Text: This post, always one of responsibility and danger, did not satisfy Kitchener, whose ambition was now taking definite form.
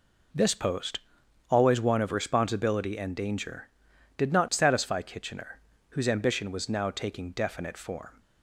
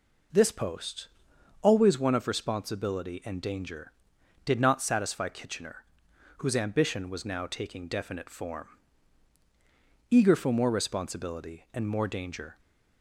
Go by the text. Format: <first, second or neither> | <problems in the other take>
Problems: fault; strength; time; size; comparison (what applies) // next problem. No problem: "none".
first | goes on to say "Eager for more responsibility and more danger"; strong; from 10.1 s on; 2.4 s long